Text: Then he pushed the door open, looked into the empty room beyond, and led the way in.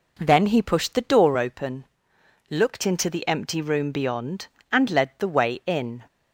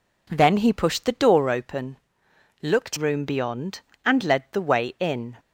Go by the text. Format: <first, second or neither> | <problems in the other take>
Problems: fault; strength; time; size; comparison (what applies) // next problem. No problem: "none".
first | skips "into the empty"; at 2.9 s